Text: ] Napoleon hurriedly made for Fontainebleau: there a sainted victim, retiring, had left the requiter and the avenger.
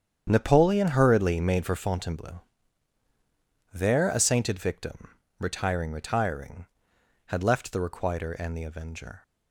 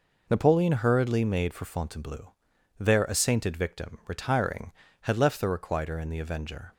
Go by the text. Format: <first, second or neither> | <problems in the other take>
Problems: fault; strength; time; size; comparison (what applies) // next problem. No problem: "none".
second | starts louder than the rest; strong; until 1.3 s; 8.5 dB // says "retiring" twice; at 5.9 s